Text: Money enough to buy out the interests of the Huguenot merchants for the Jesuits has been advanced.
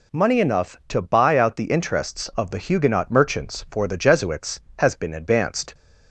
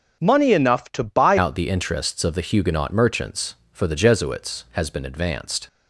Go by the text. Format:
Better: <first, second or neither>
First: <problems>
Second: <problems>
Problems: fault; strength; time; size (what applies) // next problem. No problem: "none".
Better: first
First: none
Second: starts louder than the rest; until 1.2 s; 6 dB // changes voice at "out"; from 1.3 s on; 4.3 s long